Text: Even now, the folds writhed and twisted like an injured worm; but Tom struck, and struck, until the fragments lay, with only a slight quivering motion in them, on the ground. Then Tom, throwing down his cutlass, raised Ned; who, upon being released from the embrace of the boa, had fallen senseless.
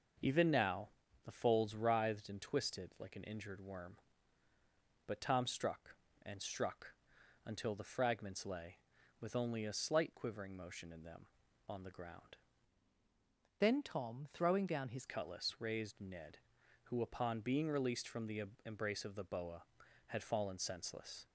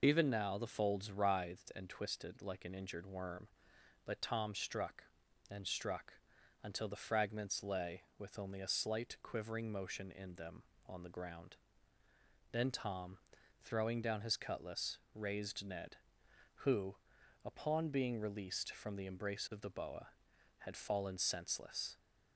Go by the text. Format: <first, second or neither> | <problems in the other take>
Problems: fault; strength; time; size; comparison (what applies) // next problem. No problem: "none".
second | changes voice from "Then" to "his"; from 13.5 to 15.0 s; 1.5 s long // pauses between "the" and "embrace"; slight; at 18.4 s; 0.24 s long